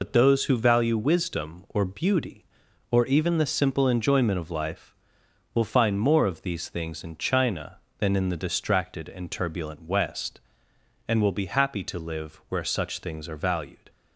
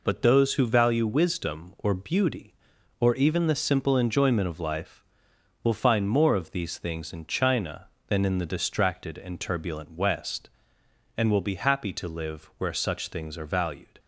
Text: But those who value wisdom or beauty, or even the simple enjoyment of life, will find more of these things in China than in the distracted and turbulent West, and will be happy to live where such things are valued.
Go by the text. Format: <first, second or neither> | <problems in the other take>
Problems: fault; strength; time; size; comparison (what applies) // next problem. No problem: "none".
second | loses the start of "But"; at 0.0 s; 70 ms